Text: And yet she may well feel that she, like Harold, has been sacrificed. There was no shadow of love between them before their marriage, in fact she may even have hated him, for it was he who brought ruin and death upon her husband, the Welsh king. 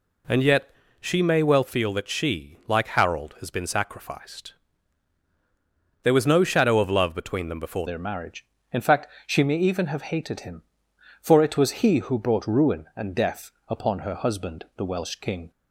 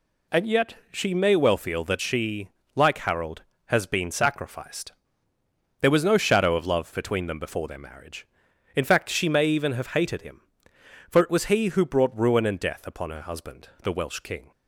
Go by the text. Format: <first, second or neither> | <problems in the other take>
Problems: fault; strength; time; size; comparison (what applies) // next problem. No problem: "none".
second | pauses between "yet" and "she"; slight; at 0.6 s; 0.30 s long; slight in the second // changes voice at "their"; from 7.8 s on; 7.7 s long // pauses between "fact" and "she"; slight; at 9.0 s; 0.20 s long // pauses between "death" and "upon"; slight; at 13.5 s; 0.18 s long